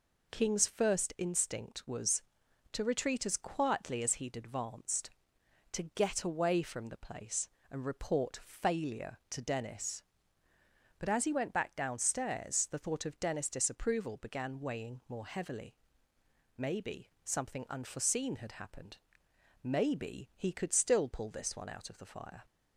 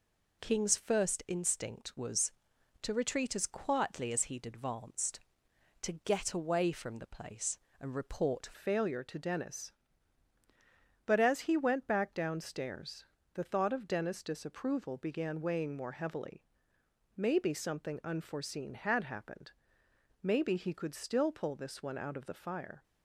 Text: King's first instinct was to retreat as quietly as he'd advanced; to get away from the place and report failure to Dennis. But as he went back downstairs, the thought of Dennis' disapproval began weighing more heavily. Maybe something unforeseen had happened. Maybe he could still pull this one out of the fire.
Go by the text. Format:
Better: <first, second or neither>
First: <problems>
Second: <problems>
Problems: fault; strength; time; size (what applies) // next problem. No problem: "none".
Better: first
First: none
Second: changes voice at "failure"; from 8.5 s on; 14.3 s long